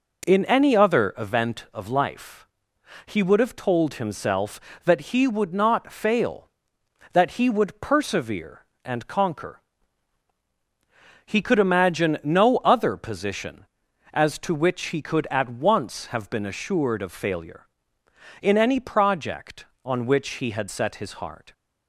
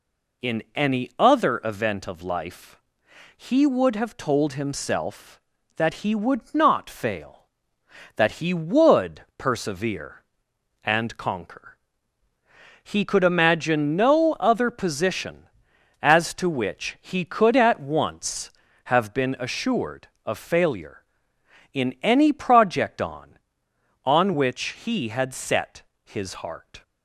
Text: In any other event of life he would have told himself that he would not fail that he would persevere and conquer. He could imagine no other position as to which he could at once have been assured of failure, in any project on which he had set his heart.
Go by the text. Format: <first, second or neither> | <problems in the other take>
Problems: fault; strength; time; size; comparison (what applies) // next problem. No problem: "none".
first | pauses between "life" and "he"; noticeable; at 2.7 s; 0.56 s long; noticeable in the first // says "on" twice; at 24.0 s // pauses between "set" and "his"; slight; at 25.8 s; 0.24 s long